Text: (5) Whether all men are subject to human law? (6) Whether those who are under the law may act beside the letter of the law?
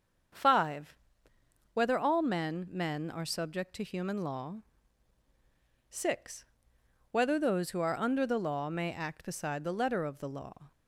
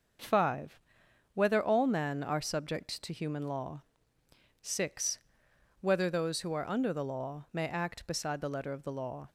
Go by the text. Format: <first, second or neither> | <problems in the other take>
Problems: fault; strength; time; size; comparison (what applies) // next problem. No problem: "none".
second | starts louder than the rest; strong; until 2.1 s; 7 dB; also in the second // says "men" twice; at 2.7 s